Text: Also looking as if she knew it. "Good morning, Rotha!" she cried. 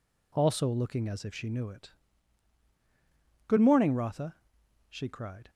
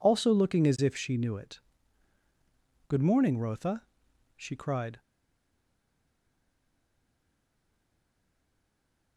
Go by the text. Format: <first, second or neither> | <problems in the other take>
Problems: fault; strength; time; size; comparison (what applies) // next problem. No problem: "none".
first | stays silent after the last word; strong; from 4.9 s on; 4.2 s long